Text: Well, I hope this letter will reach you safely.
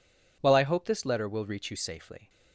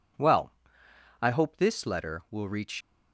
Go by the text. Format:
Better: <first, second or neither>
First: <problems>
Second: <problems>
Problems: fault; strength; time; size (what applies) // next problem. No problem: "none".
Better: first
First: none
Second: stops before "you safely"; at 2.7 s